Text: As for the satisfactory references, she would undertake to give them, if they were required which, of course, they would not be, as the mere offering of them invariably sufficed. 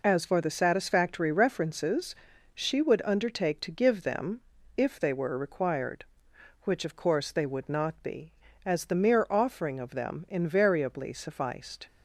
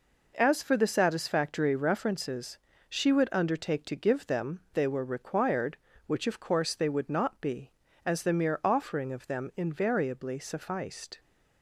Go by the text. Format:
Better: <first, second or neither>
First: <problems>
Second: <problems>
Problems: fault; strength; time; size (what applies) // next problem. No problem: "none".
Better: first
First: none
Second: skips "if"; at 4.6 s